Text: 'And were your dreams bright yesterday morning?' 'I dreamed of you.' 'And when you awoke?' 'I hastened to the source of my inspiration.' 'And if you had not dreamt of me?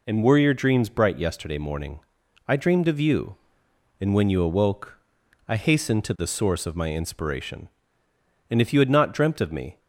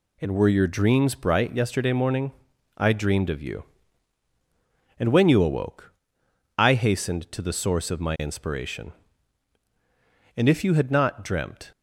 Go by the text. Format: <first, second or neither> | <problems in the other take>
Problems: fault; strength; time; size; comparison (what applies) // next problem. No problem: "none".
first | stops before "of me"; at 11.7 s